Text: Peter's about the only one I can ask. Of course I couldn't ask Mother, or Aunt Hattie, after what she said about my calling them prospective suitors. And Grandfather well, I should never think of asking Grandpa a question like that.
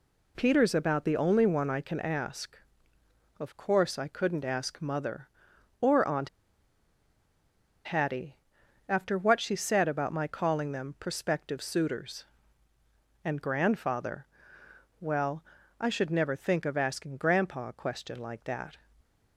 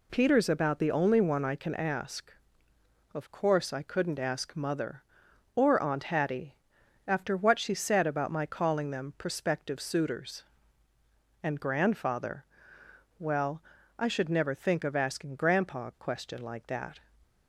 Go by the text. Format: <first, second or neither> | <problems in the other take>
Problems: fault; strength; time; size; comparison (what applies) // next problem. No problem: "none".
second | pauses between "Aunt" and "Hattie"; strong; at 6.2 s; 1.5 s long // pauses between "Grandfather" and "well"; noticeable; at 14.2 s; 0.76 s long; noticeable in the second